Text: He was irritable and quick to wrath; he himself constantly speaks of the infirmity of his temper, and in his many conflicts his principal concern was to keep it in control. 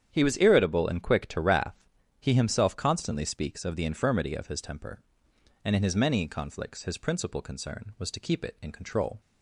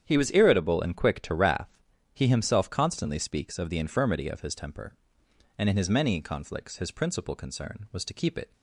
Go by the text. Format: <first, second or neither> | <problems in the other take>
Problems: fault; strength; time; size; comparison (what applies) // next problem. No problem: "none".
first | starts louder than the rest; strong; until 1.1 s; 9 dB; strong in the first // stops before "in control"; at 8.5 s